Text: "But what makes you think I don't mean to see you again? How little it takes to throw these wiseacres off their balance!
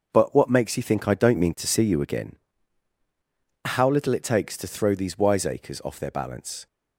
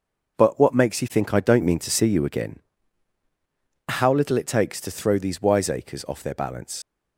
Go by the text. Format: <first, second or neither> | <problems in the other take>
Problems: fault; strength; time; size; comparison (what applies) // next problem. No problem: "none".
first | starts louder than the rest; noticeable; until 1.4 s; 6 dB; also in the first // leaves "balance" unfinished; at 6.8 s; 80 ms